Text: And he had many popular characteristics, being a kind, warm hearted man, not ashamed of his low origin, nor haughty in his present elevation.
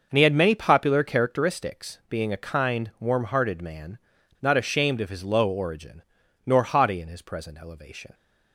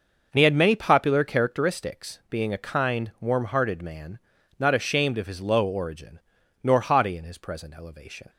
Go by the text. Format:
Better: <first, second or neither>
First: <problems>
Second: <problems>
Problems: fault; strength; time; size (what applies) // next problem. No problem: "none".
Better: neither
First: none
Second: none